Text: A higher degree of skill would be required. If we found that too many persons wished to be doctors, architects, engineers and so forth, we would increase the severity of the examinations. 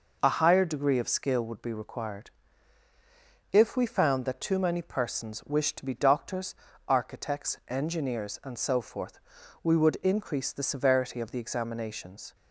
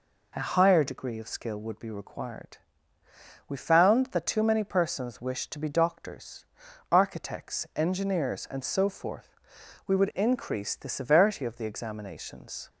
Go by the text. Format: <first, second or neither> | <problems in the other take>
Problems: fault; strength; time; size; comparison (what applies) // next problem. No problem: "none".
first | skips "If"; at 3.0 s